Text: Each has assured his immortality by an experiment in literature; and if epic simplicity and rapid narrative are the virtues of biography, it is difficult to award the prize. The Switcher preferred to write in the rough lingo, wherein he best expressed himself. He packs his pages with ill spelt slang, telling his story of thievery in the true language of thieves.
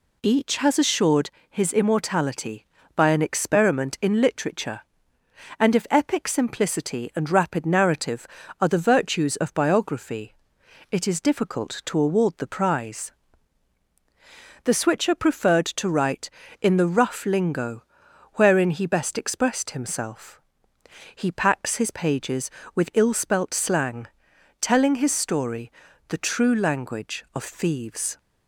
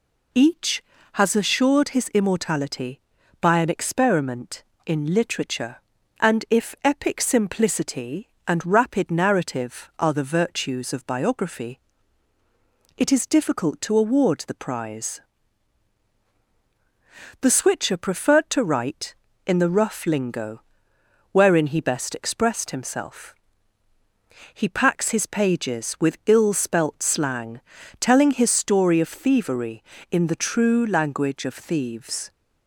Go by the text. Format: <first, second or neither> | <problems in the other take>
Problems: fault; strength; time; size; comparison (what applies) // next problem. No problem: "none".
second | pauses between "assured" and "his"; slight; at 1.2 s; 0.20 s long // skips "of thievery in"; at 25.9 s